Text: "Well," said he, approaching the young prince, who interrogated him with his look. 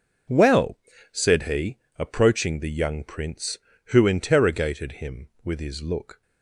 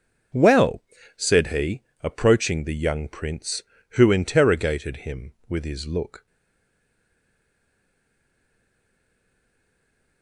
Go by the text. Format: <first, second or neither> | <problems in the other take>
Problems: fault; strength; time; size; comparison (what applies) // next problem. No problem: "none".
first | stays silent after the last word; strong; from 6.2 s on; 4.0 s long